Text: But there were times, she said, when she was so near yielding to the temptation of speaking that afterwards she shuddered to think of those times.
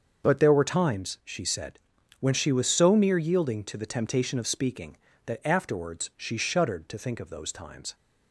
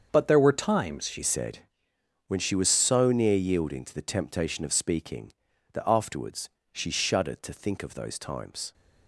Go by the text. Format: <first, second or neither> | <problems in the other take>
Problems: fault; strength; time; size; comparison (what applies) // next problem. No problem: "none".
first | starts louder than the rest; until 1.1 s; 7 dB; also in the first // changes voice at "said"; from 1.2 s on; 7.5 s long // pauses between "afterwards" and "she"; slight; at 6.4 s; 0.22 s long